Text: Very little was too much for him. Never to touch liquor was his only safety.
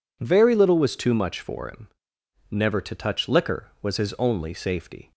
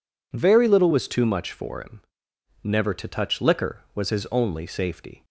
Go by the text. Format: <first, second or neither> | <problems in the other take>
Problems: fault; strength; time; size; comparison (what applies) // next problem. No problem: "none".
neither | none